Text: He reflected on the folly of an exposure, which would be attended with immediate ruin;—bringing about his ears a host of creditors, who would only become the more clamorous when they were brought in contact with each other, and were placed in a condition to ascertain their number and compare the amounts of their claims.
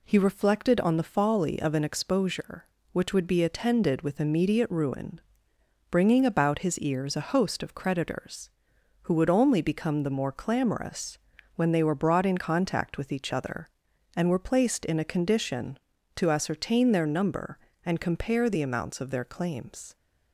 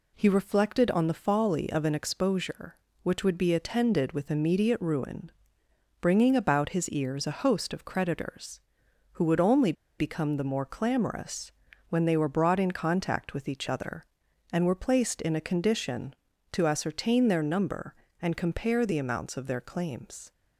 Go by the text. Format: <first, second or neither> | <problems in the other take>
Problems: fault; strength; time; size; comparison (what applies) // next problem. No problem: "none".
first | pauses between "only" and "become"; slight; at 9.7 s; 0.25 s long // pauses between "clamorous" and "when"; at 11.5 s; 0.38 s long; also in the first